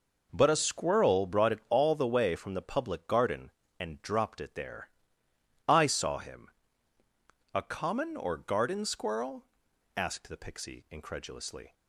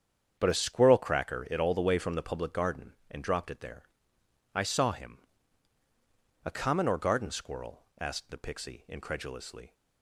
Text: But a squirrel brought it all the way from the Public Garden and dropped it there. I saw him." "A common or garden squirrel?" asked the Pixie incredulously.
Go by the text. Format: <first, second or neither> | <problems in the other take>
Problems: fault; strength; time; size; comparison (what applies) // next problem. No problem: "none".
first | starts louder than the rest; strong; until 1.4 s; 8 dB // says "cracker" for "brought"; at 0.9 s